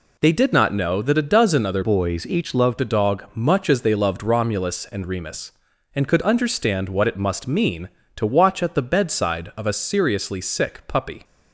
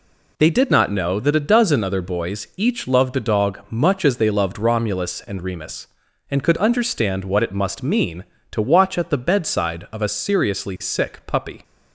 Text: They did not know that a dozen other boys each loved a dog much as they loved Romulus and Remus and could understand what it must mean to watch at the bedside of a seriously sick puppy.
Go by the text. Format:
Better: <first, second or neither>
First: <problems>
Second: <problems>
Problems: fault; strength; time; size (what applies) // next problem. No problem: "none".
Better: second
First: changes voice from "boys" to "loved"; from 1.8 to 2.7 s; 0.9 s long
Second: none